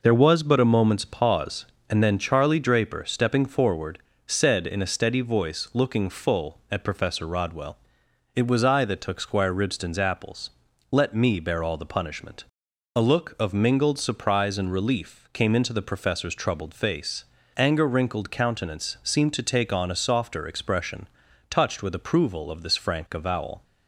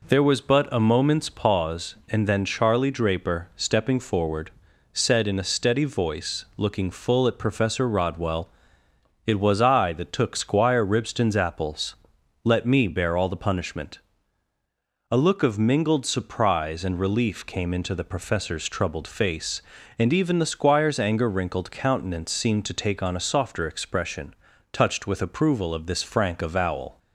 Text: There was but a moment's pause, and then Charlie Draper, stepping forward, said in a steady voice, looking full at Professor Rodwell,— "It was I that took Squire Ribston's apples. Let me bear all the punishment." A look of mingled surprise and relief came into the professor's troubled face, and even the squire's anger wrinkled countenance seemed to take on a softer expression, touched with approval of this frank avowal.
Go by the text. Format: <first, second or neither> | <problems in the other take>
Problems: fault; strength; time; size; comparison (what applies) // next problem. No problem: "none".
second | skips "and even the squire's"; at 17.3 s